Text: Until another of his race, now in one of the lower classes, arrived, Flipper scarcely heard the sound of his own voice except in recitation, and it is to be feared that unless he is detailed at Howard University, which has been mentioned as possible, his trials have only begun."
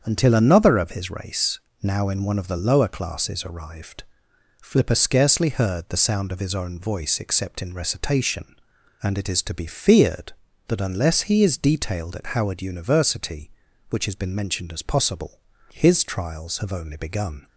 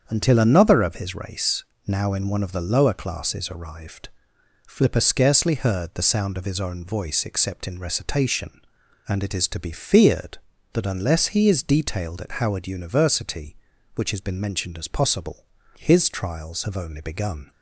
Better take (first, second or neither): neither